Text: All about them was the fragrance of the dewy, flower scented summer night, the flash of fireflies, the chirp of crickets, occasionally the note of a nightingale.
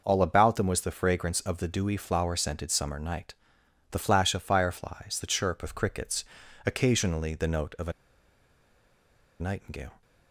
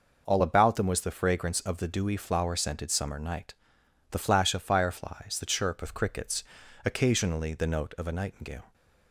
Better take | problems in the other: second | pauses between "a" and "nightingale"; strong; at 7.9 s; 1.4 s long

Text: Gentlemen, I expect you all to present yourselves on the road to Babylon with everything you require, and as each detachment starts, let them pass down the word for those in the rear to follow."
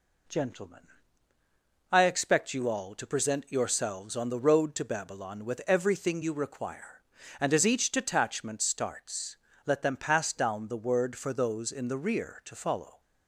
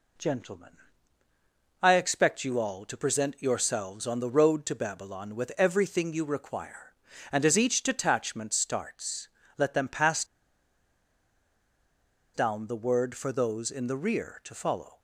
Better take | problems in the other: first | pauses between "pass" and "down"; strong; at 10.2 s; 2.1 s long

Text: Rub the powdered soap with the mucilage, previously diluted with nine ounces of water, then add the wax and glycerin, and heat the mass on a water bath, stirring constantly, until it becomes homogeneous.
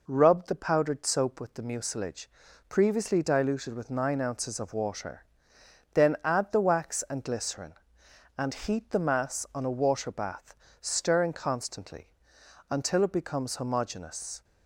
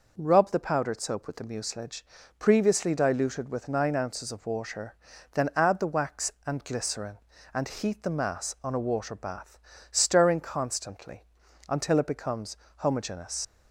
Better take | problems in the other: first | pauses between "becomes" and "homogeneous"; slight; at 12.5 s; 0.22 s long // leaves "homogeneous" unfinished; at 13.4 s; 65 ms

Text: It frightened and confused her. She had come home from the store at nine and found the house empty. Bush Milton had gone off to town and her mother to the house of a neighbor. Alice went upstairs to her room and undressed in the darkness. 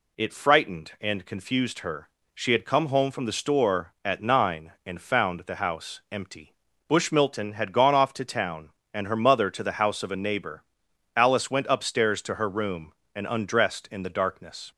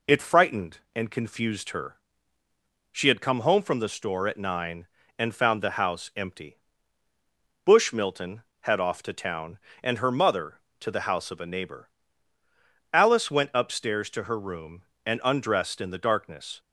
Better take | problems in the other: first | skips "gone"; at 8.7 s

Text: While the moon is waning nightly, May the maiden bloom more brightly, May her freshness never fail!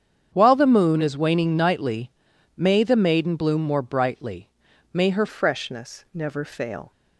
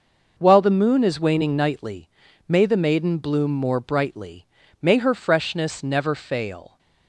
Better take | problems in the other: second | starts louder than the rest; strong; until 1.3 s; 8 dB // changes voice at "freshness"; from 5.2 s on; 1.7 s long

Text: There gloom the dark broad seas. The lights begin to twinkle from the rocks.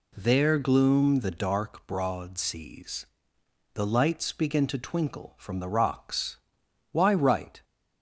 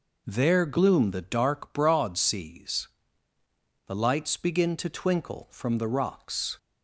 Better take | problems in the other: second | goes on to say "Why write"; noticeable; from 6.9 s on; 0.72 s long

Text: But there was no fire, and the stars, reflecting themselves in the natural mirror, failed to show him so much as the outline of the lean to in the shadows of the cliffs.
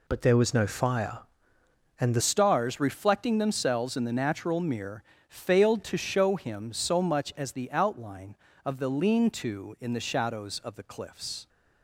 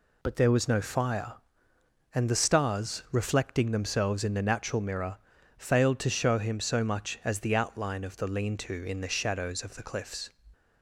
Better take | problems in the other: second | changes voice at "stars"; from 2.2 s on; 9.2 s long

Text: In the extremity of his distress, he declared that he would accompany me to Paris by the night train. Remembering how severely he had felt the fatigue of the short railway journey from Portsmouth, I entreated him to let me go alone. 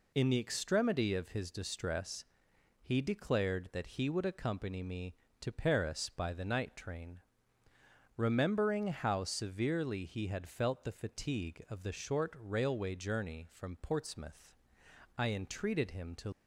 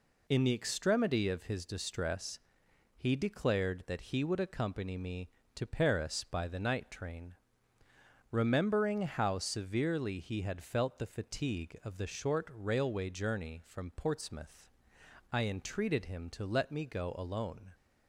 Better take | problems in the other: second | stops before "let me go alone"; at 16.3 s

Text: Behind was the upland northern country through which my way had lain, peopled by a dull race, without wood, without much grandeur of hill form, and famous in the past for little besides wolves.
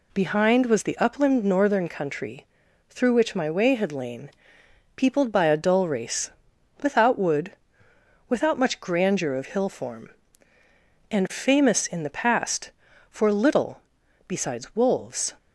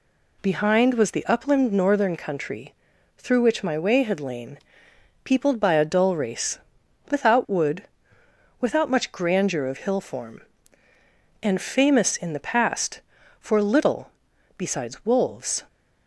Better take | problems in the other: neither | pauses between "country" and "through"; the same in both // pauses between "little" and "besides"; noticeable; the same in both

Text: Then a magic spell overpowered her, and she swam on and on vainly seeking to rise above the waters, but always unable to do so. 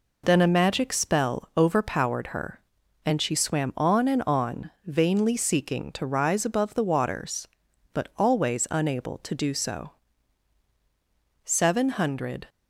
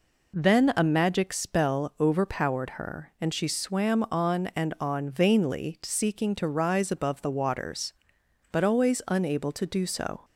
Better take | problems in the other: second | pauses between "on" and "vainly"; slight; at 4.7 s; 0.16 s long // goes on to say "Seven hundred"; noticeable; from 11.4 s on; 1.0 s long

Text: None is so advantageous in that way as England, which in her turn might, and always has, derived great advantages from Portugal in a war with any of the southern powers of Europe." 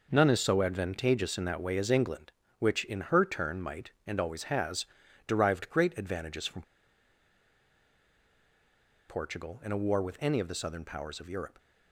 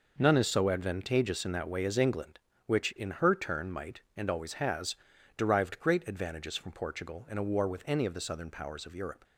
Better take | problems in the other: second | pauses between "from" and "Portugal"; strong; at 6.6 s; 2.4 s long

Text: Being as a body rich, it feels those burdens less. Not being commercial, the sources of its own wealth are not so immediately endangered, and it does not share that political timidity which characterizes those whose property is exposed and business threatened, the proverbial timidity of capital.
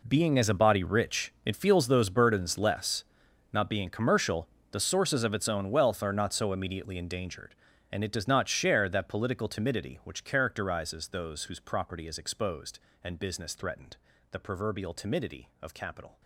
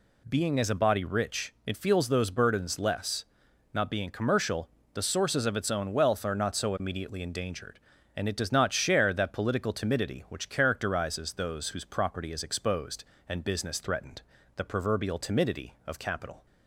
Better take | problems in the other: second | gets quieter; strong; throughout; 16 dB

